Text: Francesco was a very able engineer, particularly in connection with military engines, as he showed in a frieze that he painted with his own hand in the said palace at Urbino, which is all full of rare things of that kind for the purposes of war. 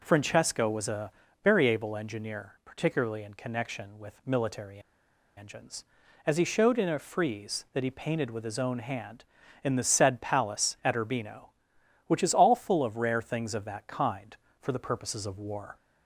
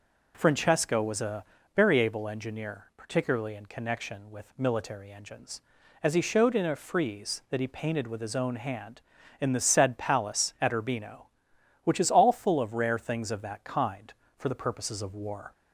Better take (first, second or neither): second